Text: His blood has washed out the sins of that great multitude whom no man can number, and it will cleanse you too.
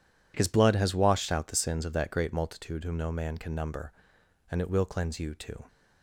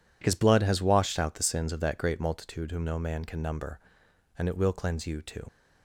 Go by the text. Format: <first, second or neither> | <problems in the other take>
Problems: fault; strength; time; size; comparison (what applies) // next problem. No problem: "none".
first | leaves "too" unfinished; at 5.4 s; 55 ms